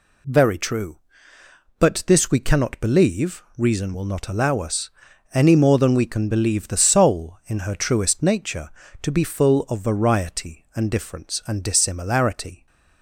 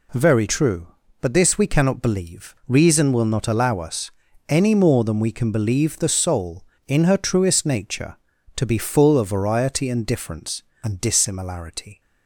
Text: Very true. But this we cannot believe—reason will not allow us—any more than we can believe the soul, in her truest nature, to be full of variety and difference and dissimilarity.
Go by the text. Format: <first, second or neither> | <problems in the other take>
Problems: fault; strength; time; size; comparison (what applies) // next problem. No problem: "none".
neither | none